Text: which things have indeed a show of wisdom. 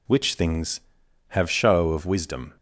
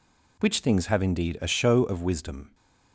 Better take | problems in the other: second | skips "indeed a"; at 1.5 s

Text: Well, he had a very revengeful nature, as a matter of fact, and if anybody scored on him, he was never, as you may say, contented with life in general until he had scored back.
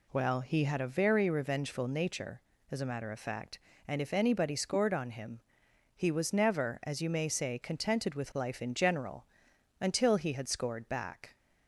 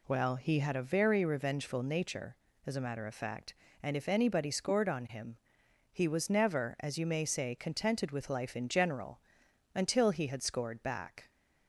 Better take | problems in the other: neither | pauses between "general" and "until"; noticeable; the same in both

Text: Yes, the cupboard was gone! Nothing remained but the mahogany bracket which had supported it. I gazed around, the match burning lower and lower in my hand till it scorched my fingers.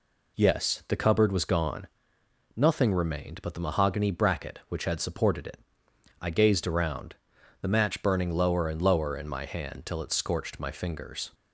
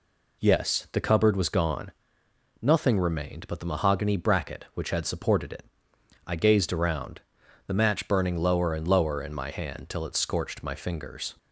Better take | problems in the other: neither | none

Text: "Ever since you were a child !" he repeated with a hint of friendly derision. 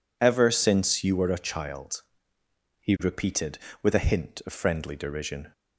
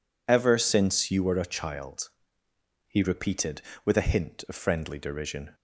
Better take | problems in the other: neither | none

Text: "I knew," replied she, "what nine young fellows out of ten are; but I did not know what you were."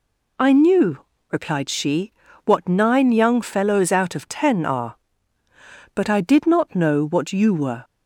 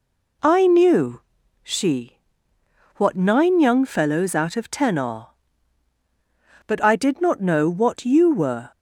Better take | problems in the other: first | skips "replied"; at 1.4 s

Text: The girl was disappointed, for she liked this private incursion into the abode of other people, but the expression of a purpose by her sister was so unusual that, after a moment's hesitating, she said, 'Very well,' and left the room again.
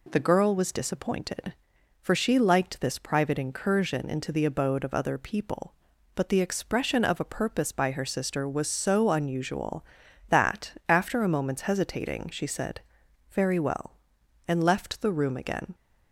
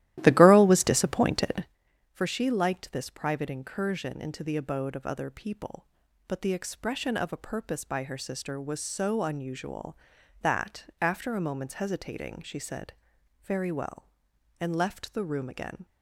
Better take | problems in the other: first | starts louder than the rest; strong; until 1.8 s; 14.5 dB

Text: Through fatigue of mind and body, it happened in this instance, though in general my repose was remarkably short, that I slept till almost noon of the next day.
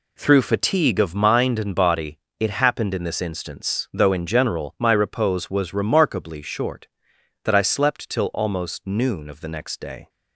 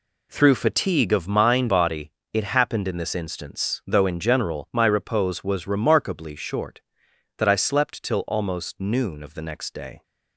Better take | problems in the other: first | skips "and"; at 1.6 s

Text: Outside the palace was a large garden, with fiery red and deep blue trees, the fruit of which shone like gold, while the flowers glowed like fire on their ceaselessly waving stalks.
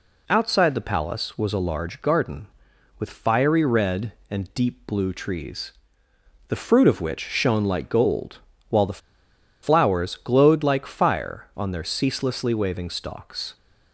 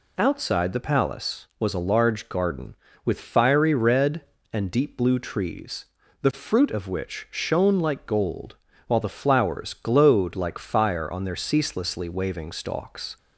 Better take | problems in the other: second | pauses between "the" and "flowers"; noticeable; at 9.0 s; 0.63 s long

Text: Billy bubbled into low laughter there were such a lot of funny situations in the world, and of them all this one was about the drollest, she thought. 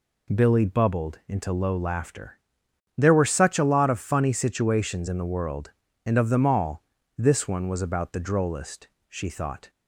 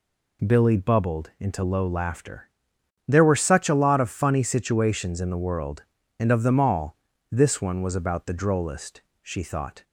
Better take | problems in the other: neither | pauses between "laughter" and "there"; noticeable; the same in both // pauses between "all" and "this"; slight; the same in both

